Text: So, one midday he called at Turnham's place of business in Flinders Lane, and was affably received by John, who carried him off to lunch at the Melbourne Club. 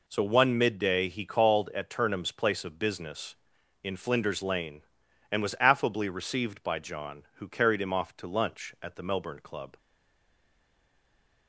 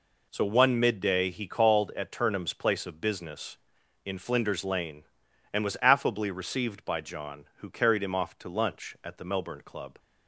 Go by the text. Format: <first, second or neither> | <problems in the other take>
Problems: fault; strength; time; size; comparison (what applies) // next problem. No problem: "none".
second | stays silent after the last word; noticeable; from 9.7 s on; 1.7 s long